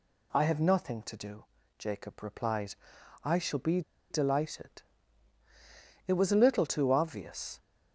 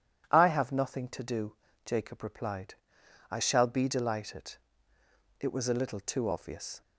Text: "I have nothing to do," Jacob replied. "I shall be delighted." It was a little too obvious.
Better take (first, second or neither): second